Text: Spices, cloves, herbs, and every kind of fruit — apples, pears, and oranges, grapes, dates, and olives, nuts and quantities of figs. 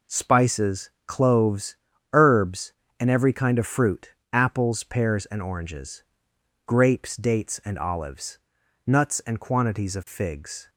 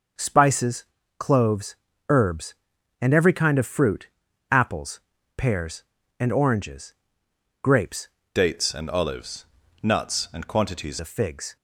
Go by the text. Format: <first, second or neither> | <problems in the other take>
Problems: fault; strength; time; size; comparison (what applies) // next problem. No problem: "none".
first | changes voice from "dates" to "quantities"; from 8.3 to 10.9 s; 2.6 s long